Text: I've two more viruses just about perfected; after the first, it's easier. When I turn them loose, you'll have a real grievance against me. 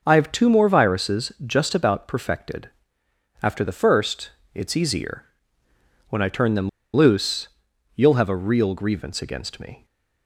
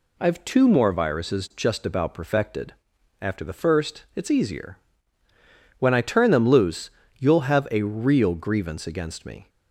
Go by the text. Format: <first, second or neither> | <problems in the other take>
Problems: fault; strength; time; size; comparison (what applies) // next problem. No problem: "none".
second | starts louder than the rest; noticeable; until 1.0 s; 6 dB // pauses between "them" and "loose"; slight; at 6.6 s; 0.25 s long